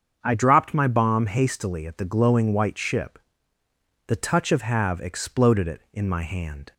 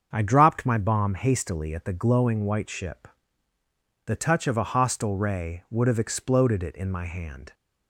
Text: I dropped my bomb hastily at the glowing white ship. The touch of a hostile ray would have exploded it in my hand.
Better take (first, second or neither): second